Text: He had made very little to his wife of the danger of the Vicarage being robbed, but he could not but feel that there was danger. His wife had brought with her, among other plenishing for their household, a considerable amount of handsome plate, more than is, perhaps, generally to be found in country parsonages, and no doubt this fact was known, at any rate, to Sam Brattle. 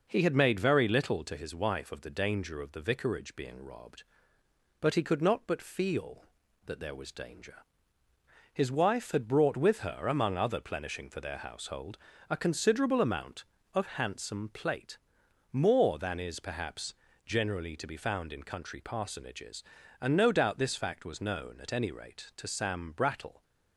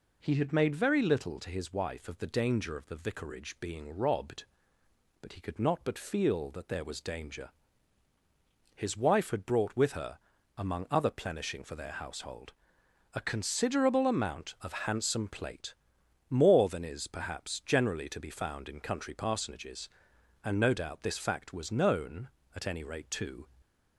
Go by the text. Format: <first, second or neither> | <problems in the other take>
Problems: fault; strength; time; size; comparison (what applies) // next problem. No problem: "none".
first | stops before "Sam Brattle"; at 23.6 s